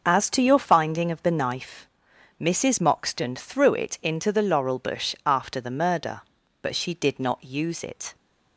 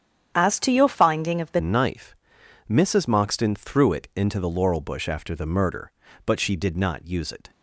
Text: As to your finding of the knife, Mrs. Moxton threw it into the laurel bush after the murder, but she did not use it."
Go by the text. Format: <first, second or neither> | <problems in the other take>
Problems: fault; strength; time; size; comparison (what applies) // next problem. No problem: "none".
first | starts louder than the rest; strong; until 1.3 s; 9 dB; noticeable in the first // changes voice at "knife"; from 1.5 s on; 6.0 s long